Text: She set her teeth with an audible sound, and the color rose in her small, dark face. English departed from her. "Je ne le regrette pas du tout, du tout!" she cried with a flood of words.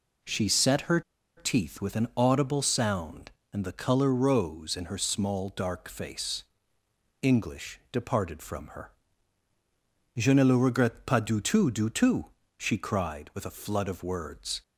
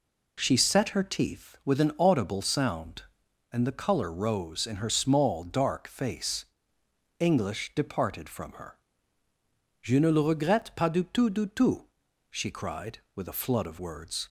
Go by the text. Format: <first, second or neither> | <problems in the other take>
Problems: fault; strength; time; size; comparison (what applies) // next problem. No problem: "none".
second | pauses between "her" and "teeth"; at 1.0 s; 0.36 s long